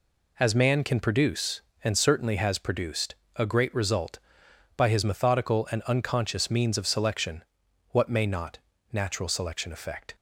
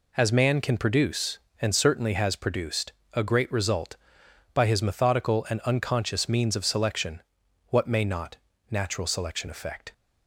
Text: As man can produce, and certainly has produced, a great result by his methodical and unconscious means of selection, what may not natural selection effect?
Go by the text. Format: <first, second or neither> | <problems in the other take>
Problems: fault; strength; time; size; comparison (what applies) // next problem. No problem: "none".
neither | pauses between "not" and "natural"; slight; the same in both